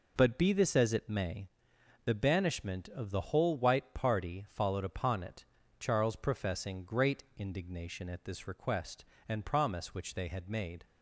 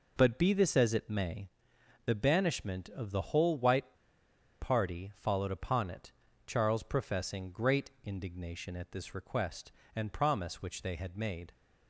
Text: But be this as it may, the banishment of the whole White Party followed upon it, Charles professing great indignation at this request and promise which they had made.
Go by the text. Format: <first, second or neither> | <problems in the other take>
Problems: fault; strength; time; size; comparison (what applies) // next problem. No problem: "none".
first | pauses between "White" and "Party"; noticeable; at 3.9 s; 0.67 s long